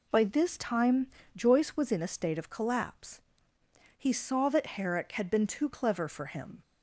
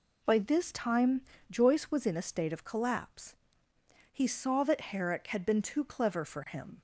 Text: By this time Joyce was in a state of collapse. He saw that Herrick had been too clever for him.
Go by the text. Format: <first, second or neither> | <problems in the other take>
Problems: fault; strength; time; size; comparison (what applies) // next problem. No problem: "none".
neither | pauses between "time" and "Joyce"; slight; the same in both